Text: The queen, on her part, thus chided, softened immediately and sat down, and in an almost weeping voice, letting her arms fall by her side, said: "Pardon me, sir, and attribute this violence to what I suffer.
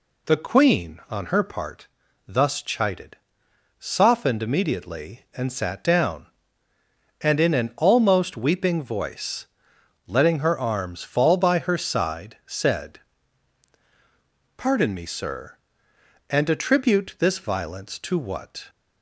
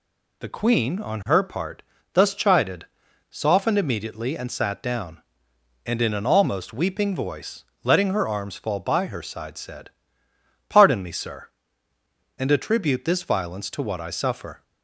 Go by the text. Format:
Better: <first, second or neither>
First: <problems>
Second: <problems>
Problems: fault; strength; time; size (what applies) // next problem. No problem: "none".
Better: second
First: stops before "I suffer"; at 18.6 s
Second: none